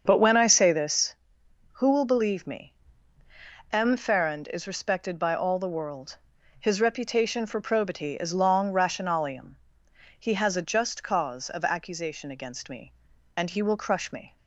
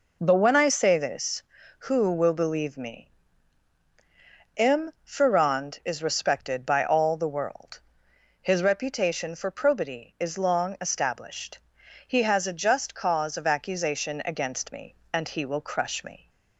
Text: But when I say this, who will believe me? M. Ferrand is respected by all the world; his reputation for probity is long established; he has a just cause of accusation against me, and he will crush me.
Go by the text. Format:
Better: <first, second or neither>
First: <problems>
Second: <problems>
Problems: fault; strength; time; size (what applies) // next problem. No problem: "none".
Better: second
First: starts louder than the rest; until 1.0 s; 7 dB // says "rationalium" for "established"; at 8.7 s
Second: none